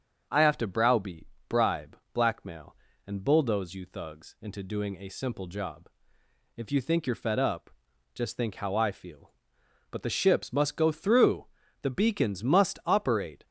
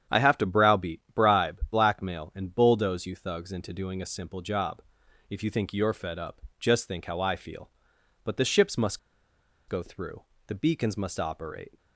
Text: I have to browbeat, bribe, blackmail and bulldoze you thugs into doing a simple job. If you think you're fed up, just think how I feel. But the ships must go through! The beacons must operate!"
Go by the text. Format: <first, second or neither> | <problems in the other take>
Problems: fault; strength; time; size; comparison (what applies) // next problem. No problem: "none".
first | starts louder than the rest; strong; until 1.2 s; 9 dB; also in the first // pauses between "must" and "go"; noticeable; at 8.9 s; 0.71 s long